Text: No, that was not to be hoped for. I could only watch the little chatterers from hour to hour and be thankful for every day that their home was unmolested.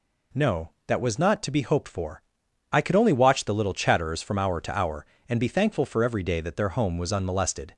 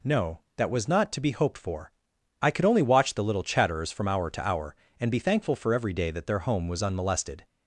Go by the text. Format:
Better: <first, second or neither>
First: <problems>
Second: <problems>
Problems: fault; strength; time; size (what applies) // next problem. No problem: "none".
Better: neither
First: none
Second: none